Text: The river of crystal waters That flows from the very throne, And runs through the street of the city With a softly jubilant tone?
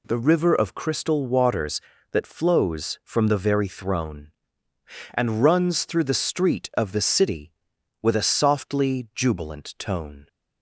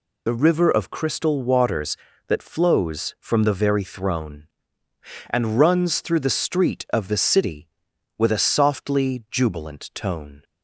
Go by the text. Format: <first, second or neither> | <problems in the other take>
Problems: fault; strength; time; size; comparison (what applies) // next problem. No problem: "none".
first | loses the start of "The"; at 0.2 s; 50 ms